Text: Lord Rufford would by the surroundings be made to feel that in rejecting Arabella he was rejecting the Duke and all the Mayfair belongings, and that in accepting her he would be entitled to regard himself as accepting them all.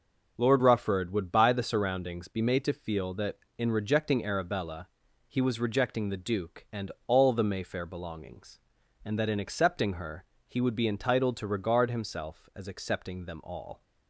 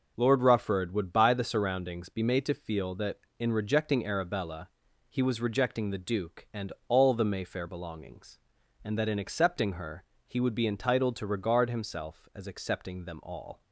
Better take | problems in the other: neither | pauses between "Arabella" and "he"; the same in both // pauses between "and" and "all"; slight; the same in both // pauses between "her" and "he"; slight; the same in both

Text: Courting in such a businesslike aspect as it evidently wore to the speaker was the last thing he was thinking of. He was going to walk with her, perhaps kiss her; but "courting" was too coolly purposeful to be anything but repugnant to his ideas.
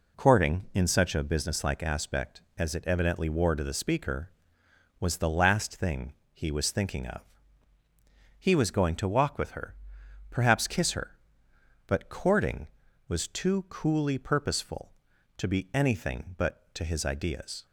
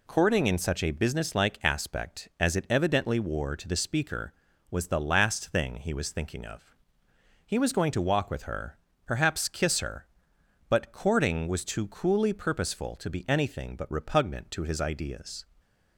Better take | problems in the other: second | pauses between "thing" and "he"; slight; at 6.1 s; 0.20 s long // skips "repugnant"; at 16.7 s

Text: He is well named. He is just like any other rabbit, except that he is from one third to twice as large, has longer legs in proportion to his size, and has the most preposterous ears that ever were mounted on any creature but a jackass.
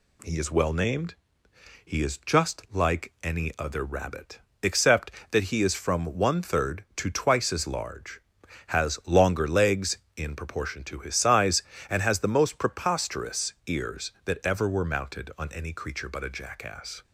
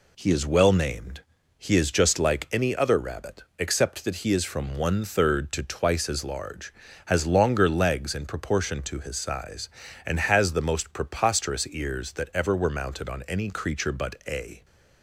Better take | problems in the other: first | stops before "jackass"; at 14.6 s

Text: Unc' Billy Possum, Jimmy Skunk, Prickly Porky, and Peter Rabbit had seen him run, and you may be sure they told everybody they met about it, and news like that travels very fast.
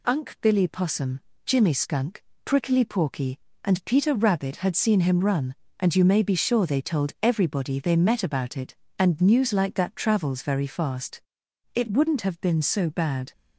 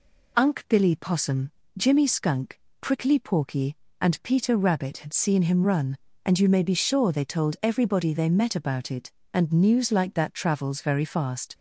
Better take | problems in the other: second | goes on to say "It wouldn't have been so bad"; from 11.7 s on; 1.5 s long

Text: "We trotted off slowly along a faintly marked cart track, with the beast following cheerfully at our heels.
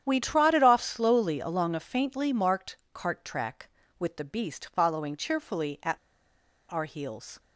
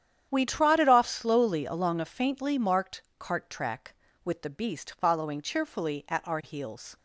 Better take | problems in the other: second | starts louder than the rest; strong; until 1.0 s; 9.5 dB; strong in the second // pauses between "marked" and "cart"; slight; at 2.7 s; 0.16 s long; slight in the second // pauses between "at" and "our"; noticeable; at 5.9 s; 0.73 s long

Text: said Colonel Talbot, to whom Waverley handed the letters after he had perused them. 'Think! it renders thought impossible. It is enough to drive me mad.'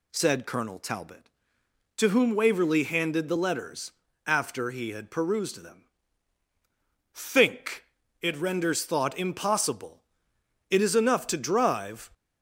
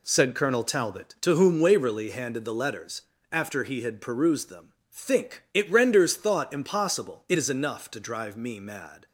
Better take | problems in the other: second | pauses between "letters" and "after"; slight; at 3.9 s; 0.34 s long; slight in the second // stops before "me mad"; at 12.1 s

